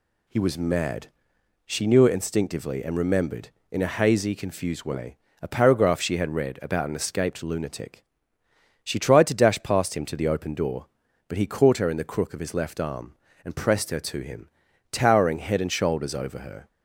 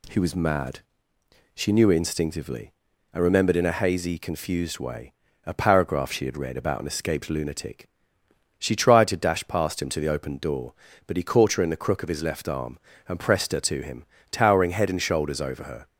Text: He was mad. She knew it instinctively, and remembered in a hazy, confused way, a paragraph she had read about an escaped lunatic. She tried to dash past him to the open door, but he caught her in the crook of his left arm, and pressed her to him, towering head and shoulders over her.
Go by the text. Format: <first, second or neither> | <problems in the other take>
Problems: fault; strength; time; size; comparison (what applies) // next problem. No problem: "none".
neither | none